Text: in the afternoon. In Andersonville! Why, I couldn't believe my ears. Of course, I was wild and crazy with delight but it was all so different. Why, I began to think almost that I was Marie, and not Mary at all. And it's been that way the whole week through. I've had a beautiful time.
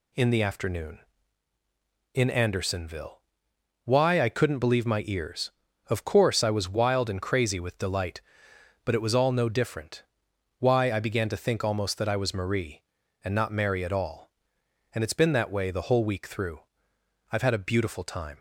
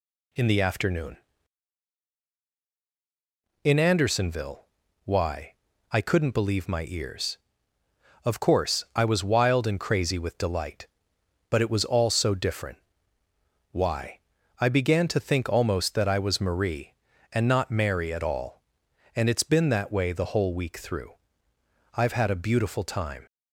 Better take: second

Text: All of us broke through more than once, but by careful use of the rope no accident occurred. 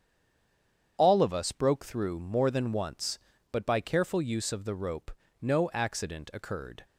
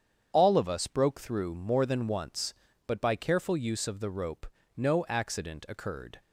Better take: second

